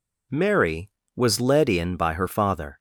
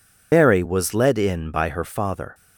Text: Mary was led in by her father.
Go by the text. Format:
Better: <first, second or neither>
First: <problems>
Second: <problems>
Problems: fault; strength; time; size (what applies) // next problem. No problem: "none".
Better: first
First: none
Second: loses the start of "Mary"; at 0.3 s; 90 ms